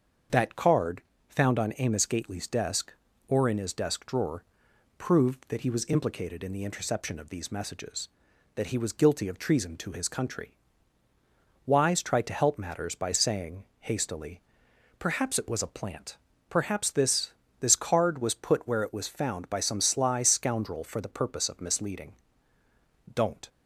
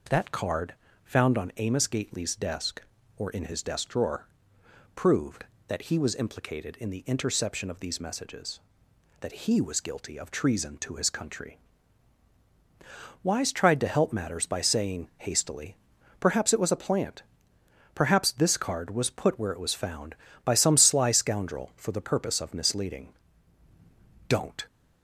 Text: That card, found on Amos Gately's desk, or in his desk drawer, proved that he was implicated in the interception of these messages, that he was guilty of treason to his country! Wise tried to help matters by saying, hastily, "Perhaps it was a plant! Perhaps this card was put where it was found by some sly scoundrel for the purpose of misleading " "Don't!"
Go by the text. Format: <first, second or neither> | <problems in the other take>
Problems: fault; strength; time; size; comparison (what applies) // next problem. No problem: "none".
second | starts louder than the rest; until 1.5 s; 7 dB // says "this" twice; at 17.6 s